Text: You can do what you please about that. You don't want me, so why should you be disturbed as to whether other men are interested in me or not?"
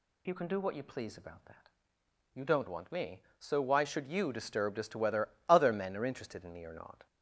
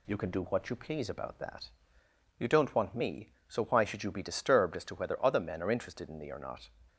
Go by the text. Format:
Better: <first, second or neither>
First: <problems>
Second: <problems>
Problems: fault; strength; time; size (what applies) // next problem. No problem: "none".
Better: second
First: skips "be"; at 4.3 s // pauses between "whether" and "other"; slight; at 5.2 s; 0.20 s long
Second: none